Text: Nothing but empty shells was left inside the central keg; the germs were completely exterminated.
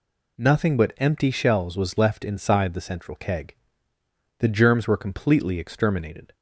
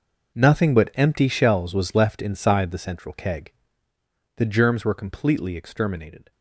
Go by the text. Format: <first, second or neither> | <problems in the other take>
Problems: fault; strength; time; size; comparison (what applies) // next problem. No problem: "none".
first | gets quieter; strong; throughout; 15 dB